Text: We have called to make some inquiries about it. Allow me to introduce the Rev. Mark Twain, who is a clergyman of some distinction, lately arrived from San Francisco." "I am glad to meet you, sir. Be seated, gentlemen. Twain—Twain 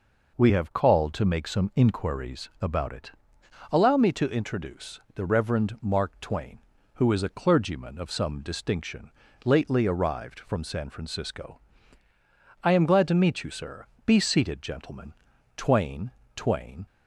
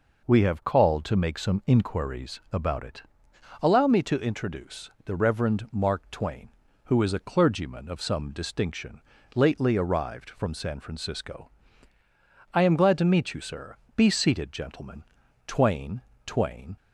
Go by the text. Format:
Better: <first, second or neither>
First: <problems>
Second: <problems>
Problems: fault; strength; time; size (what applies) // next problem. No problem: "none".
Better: neither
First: pauses between "introduce" and "the"; slight; at 4.9 s; 0.16 s long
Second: pauses between "introduce" and "the"; slight; at 4.8 s; 0.16 s long